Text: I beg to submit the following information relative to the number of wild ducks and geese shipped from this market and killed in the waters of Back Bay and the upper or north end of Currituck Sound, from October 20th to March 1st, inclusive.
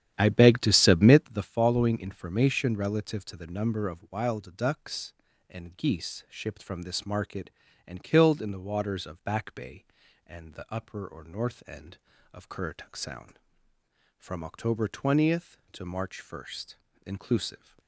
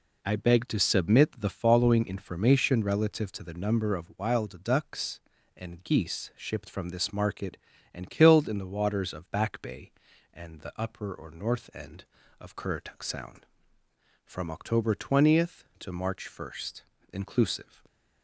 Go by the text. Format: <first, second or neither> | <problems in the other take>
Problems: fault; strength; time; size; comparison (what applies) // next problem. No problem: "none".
second | starts louder than the rest; strong; until 1.4 s; 10.5 dB